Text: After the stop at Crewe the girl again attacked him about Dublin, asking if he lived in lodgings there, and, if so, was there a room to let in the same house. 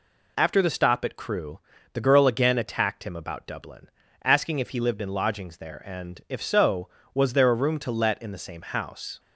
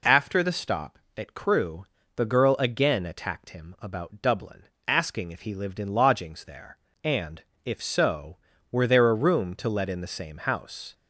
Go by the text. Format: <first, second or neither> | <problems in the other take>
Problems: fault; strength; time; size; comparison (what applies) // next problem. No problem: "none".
first | pauses between "Crewe" and "the"; slight; at 1.8 s; 0.30 s long; slight in the first // says "were" for "was"; at 8.7 s